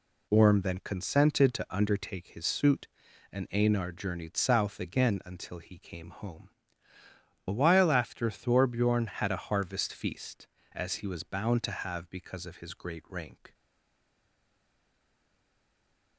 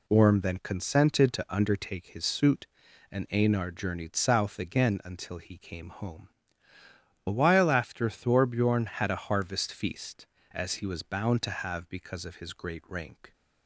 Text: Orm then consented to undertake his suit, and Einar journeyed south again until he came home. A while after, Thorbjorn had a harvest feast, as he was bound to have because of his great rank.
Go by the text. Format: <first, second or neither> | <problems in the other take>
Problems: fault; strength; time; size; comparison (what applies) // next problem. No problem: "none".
second | stays silent after the last word; strong; from 13.5 s on; 2.6 s long